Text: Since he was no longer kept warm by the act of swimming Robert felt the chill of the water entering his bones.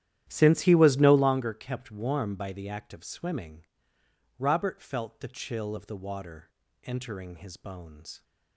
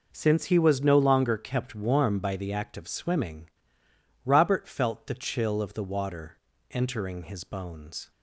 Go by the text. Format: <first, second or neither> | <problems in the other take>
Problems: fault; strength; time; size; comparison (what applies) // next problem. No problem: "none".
second | starts louder than the rest; strong; until 1.4 s; 12 dB // pauses between "swimming" and "Robert"; noticeable; at 3.6 s; 0.74 s long; noticeable in the second // pauses between "water" and "entering"; slight; at 6.5 s; 0.32 s long; slight in the second